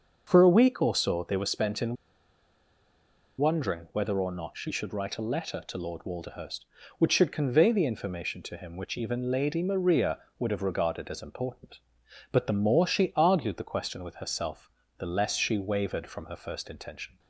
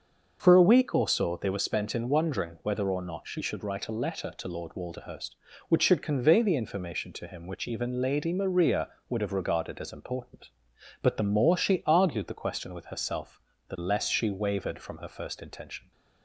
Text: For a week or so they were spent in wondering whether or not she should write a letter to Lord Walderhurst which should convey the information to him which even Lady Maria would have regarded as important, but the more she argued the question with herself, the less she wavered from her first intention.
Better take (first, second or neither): second